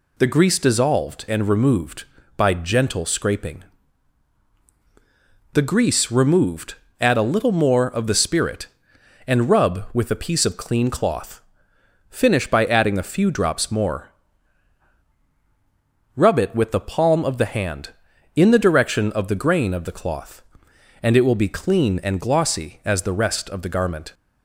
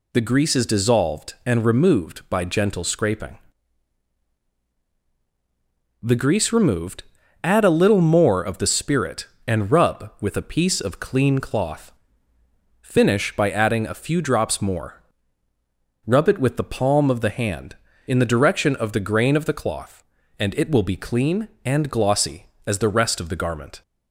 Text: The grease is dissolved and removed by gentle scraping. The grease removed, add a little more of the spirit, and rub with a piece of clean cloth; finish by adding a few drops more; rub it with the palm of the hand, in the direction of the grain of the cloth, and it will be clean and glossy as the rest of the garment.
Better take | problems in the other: second | skips "is"; at 0.5 s

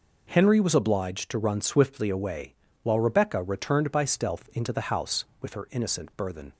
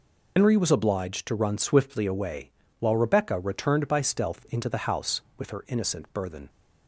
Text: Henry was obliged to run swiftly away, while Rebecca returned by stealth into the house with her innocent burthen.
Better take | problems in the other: first | loses the start of "Henry"; at 0.3 s; 125 ms

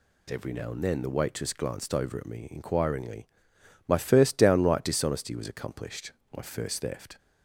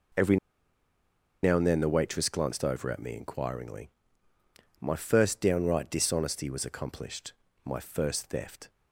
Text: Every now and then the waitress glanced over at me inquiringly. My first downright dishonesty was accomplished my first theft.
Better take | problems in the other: first | pauses between "Every" and "now"; at 0.3 s; 1.0 s long // pauses between "accomplished" and "my"; slight; at 7.3 s; 0.32 s long; slight in the first

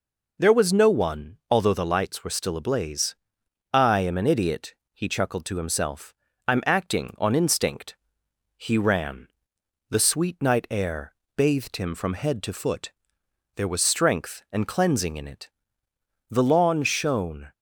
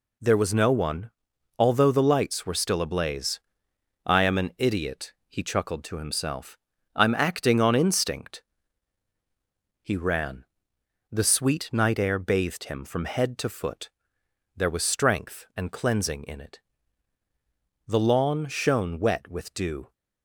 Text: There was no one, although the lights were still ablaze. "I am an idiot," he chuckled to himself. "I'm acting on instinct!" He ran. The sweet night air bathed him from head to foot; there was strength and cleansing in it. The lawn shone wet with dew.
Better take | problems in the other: second | pauses between "air" and "bathed"; slight; at 11.1 s; 0.22 s long // stops before "wet with dew"; at 17.5 s

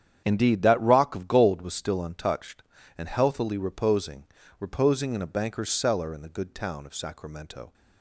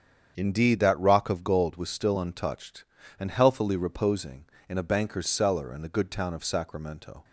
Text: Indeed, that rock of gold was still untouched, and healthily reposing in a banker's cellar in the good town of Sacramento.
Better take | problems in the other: second | starts louder than the rest; strong; until 1.2 s; 9 dB; strong in the second // says "reposing" twice; at 4.5 s

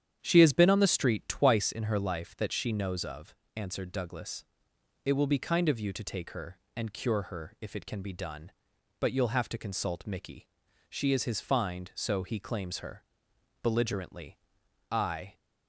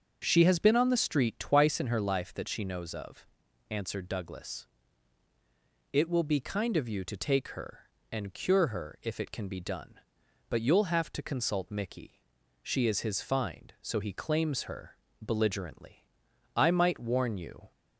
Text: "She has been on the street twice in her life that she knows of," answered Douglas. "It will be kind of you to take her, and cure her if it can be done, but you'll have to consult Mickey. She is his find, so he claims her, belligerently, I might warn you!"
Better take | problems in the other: second | starts louder than the rest; strong; until 1.2 s; 9 dB; also in the second // stops before "might warn you"; at 15.3 s

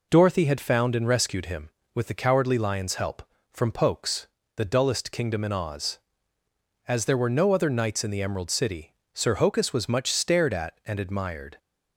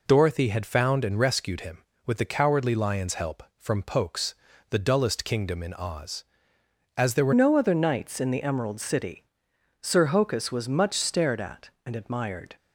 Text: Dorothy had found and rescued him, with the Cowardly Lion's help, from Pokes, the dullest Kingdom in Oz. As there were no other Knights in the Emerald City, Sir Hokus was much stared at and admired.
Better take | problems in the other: first | changes voice at "no"; from 7.3 s on; 5.2 s long

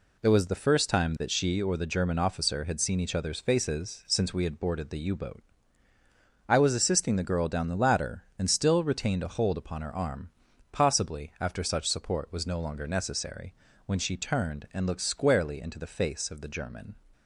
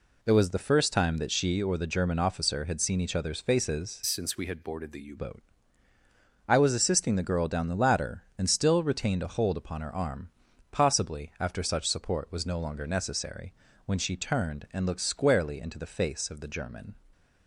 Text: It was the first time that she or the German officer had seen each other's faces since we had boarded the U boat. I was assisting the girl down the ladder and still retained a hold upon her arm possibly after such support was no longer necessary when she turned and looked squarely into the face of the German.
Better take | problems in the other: first | changes voice from "since" to "U"; from 4.0 to 5.1 s; 1.1 s long // pauses between "arm" and "possibly"; at 10.3 s; 0.42 s long; also in the first // pauses between "necessary" and "when"; slight; at 13.5 s; 0.34 s long; slight in the first

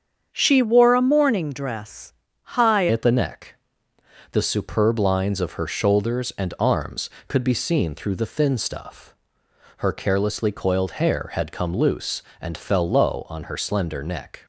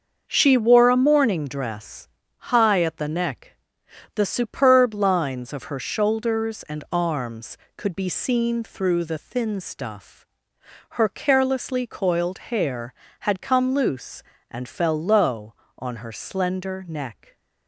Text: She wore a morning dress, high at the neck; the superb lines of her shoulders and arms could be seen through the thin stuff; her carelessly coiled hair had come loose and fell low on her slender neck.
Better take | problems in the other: second | starts louder than the rest; strong; until 1.3 s; 7.5 dB; also in the second // changes voice at "at"; from 2.9 s on; 11.5 s long

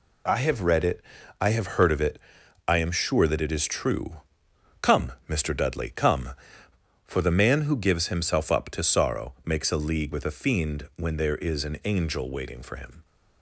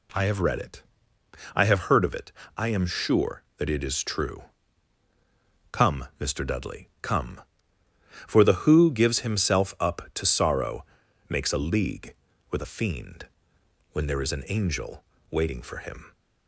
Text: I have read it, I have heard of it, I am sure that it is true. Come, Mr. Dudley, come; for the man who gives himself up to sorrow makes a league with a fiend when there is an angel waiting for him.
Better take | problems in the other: first | skips "man"; at 8.6 s // pauses between "sorrow" and "makes"; at 10.8 s; 0.44 s long // pauses between "fiend" and "when"; noticeable; at 13.2 s; 0.66 s long // pauses between "angel" and "waiting"; slight; at 15.0 s; 0.26 s long

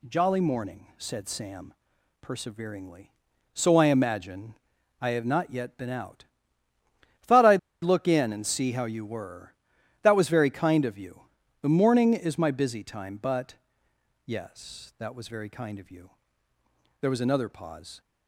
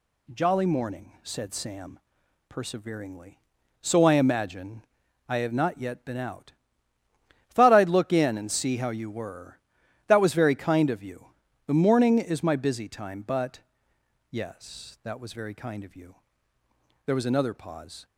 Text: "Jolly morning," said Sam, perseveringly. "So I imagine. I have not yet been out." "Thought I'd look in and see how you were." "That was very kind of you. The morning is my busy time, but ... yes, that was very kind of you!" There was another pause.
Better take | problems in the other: second | pauses between "I'd" and "look"; slight; at 7.5 s; 0.24 s long

